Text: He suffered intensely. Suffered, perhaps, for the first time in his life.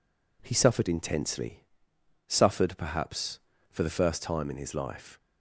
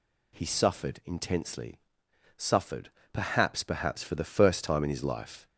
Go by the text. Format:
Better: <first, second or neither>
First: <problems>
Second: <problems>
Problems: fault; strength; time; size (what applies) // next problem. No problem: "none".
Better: first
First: none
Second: says "perhaps" twice; at 3.6 s